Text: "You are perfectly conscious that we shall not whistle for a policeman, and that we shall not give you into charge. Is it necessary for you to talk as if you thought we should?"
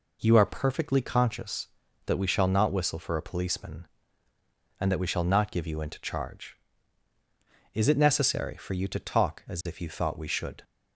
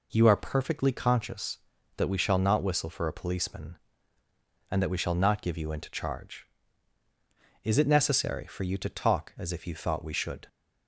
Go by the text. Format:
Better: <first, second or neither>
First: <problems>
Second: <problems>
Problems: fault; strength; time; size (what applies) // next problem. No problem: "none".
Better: neither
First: none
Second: none